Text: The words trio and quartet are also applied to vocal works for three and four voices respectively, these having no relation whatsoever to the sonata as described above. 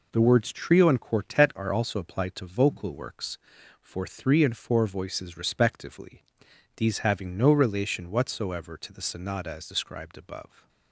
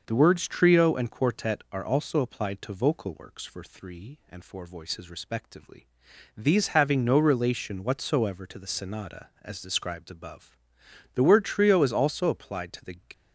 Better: first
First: none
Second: starts louder than the rest; until 1.0 s; 6 dB // goes on to say "The word trio is also applied to the"; strong; from 11.1 s on; 1.8 s long

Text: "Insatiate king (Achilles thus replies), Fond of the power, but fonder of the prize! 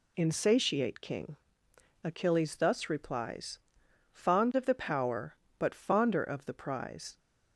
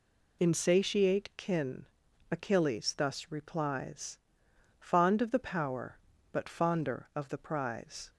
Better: first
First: none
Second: says "kin" for "king"; at 1.3 s

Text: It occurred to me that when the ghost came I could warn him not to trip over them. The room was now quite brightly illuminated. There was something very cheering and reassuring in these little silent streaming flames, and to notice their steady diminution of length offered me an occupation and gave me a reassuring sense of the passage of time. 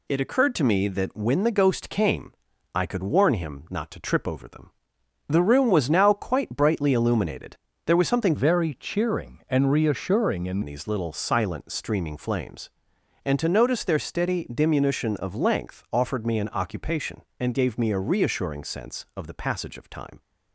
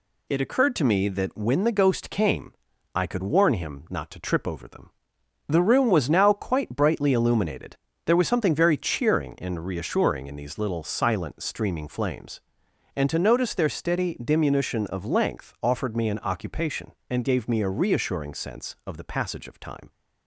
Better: second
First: pauses between "came" and "I"; at 2.3 s; 0.42 s long // changes voice from "very" to "in"; from 8.3 to 10.6 s; 2.3 s long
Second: pauses between "came" and "I"; at 2.5 s; 0.42 s long

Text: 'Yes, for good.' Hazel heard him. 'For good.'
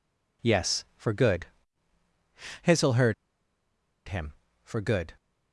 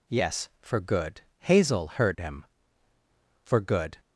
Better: second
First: pauses between "heard" and "him"; noticeable; at 3.1 s; 0.94 s long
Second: none

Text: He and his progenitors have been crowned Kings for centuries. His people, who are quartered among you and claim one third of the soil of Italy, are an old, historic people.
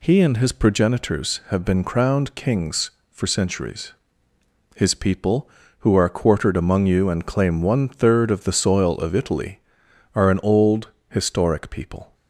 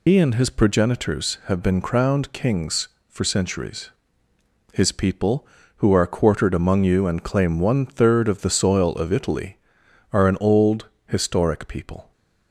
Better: first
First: none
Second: loses the start of "He"; at 0.0 s; 70 ms

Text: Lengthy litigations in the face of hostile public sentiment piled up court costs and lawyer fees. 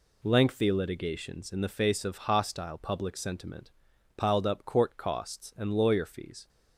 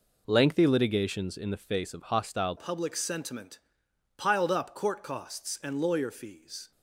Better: first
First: pauses between "sentiment" and "piled"; noticeable; at 3.7 s; 0.46 s long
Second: changes voice at "public"; from 2.5 s on; 4.2 s long // pauses between "sentiment" and "piled"; noticeable; at 3.5 s; 0.58 s long

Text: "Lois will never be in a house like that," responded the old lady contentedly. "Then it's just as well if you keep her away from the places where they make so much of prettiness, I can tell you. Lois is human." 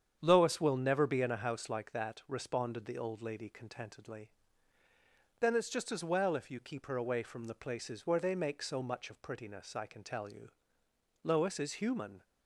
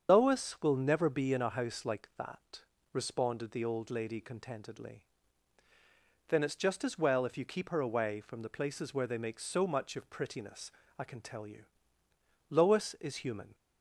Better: first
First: starts louder than the rest; strong; until 1.2 s; 8.5 dB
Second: loses the start of "Lois"; at 0.0 s; 135 ms // starts louder than the rest; strong; until 1.1 s; 7 dB

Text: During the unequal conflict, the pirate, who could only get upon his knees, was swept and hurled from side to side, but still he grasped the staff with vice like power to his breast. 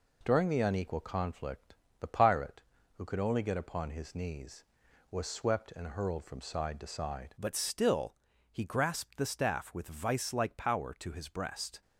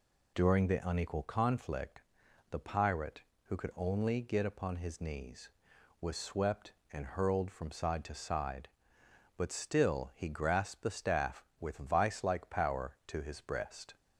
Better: second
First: changes voice at "but"; from 7.3 s on; 4.5 s long // pauses between "still" and "he"; at 8.1 s; 0.38 s long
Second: none

